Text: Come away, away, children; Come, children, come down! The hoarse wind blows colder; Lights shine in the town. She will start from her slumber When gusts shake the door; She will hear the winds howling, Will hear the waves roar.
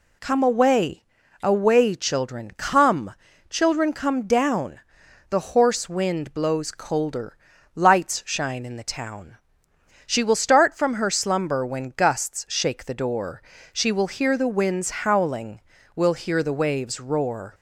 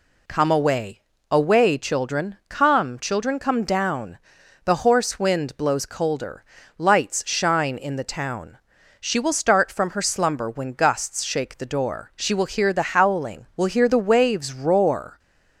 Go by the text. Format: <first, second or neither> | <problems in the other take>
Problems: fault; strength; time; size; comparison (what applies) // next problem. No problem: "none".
first | skips "winds"; at 12.9 s